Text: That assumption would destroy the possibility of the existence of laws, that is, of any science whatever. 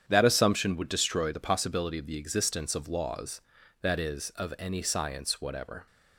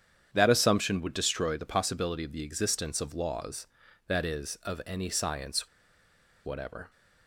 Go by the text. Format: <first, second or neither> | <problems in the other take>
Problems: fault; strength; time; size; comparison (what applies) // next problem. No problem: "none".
first | starts louder than the rest; strong; until 1.3 s; 8.5 dB; strong in the first // pauses between "science" and "whatever"; noticeable; at 5.6 s; 0.77 s long